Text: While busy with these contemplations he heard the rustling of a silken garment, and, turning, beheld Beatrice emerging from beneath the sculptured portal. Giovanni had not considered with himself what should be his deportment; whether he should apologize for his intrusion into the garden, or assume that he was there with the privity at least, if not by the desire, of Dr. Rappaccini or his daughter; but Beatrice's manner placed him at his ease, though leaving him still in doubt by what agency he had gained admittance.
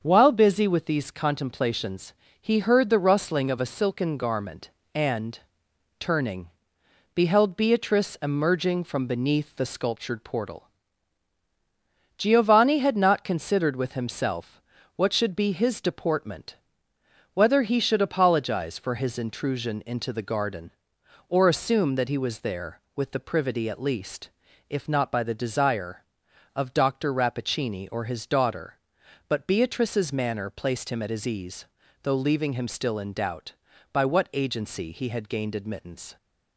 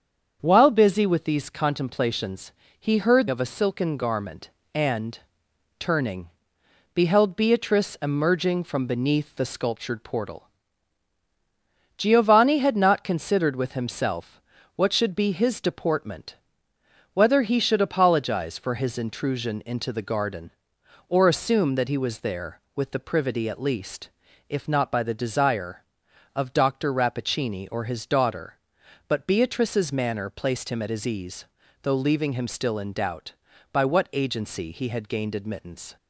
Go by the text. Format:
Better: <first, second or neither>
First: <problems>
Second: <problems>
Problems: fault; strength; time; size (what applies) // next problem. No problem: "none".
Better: first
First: starts louder than the rest; until 1.0 s; 7 dB // pauses between "contemplations" and "he"; slight; at 2.1 s; 0.28 s long // pauses between "himself" and "what"; at 14.5 s; 0.38 s long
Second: starts louder than the rest; strong; until 1.4 s; 7 dB // pauses between "contemplations" and "he"; slight; at 2.5 s; 0.28 s long // skips "the rustling"; at 3.2 s // pauses between "himself" and "what"; at 14.3 s; 0.38 s long